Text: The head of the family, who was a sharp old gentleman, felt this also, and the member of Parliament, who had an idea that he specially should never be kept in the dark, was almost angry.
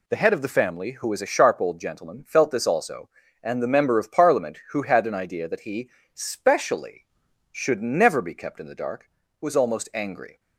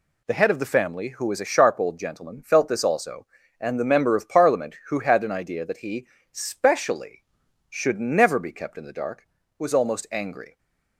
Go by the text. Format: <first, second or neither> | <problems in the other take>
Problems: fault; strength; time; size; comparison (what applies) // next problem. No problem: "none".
neither | pauses between "he" and "specially"; slight; the same in both